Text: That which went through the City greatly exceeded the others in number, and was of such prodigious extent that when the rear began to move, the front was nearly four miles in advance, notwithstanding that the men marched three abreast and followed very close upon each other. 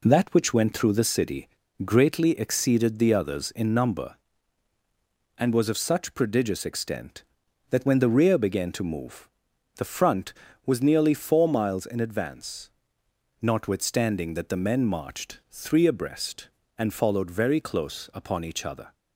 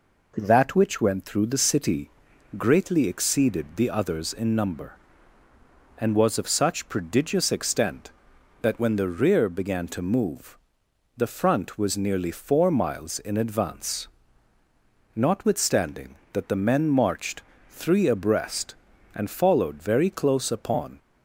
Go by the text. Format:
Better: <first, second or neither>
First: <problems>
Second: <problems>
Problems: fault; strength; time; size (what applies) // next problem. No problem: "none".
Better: first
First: pauses between "City" and "greatly"; at 1.4 s; 0.38 s long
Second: pauses between "City" and "greatly"; noticeable; at 2.0 s; 0.48 s long // pauses between "marched" and "three"; slight; at 17.4 s; 0.28 s long // stops before "each other"; at 20.9 s